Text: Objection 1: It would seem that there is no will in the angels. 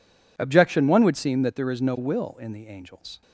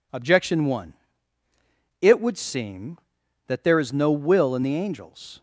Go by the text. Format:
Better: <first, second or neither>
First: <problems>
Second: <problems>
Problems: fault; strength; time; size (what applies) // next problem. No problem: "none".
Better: second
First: skips "It"; at 1.0 s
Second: none